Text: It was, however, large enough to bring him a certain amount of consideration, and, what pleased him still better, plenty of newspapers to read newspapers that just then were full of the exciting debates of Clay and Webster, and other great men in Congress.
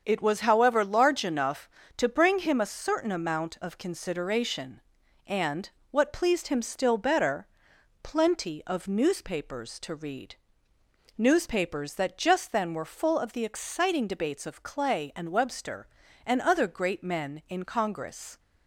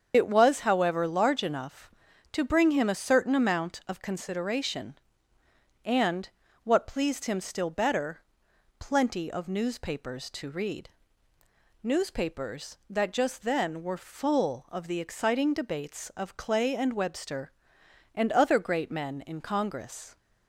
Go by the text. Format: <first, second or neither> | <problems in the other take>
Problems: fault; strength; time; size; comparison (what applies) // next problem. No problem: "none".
first | loses the start of "It"; at 0.1 s; 65 ms // starts louder than the rest; strong; until 1.1 s; 7.5 dB; also in the first // pauses between "read" and "newspapers"; noticeable; at 10.8 s; 0.92 s long; noticeable in the first